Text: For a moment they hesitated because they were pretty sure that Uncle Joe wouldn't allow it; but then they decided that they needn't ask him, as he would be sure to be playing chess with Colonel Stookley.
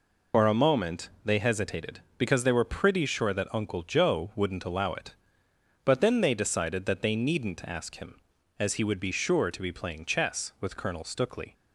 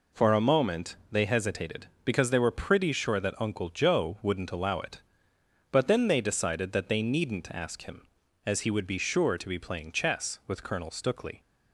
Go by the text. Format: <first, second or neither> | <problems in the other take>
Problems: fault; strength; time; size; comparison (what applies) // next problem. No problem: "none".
second | loses the start of "For"; at 0.3 s; 75 ms // pauses between "moment" and "they"; slight; at 1.0 s; 0.16 s long; slight in the second